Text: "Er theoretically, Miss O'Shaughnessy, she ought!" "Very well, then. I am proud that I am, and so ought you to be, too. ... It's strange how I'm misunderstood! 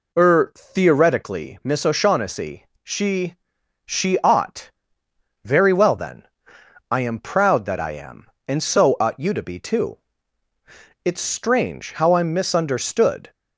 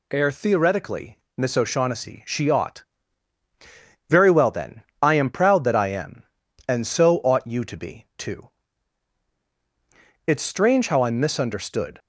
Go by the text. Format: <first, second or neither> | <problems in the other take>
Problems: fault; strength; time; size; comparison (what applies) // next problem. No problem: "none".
second | says "she" twice; at 3.8 s